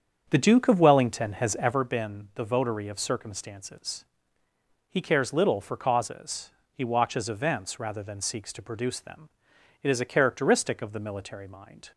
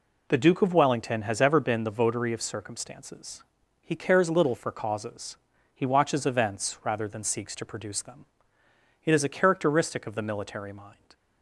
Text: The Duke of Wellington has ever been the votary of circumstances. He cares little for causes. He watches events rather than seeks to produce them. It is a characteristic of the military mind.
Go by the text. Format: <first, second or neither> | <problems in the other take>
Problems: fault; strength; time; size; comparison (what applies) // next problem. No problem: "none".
second | starts louder than the rest; strong; until 1.8 s; 7.5 dB